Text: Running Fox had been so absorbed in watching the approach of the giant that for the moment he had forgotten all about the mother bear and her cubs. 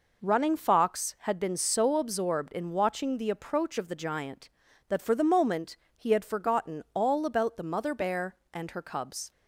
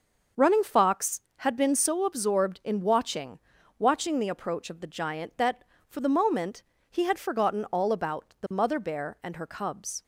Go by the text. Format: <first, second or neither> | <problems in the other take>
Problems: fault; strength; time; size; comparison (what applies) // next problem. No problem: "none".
first | starts louder than the rest; noticeable; until 1.5 s; 6 dB // says "watching" twice; at 3.7 s // pauses between "moment" and "he"; slight; at 6.6 s; 0.30 s long; slight in the first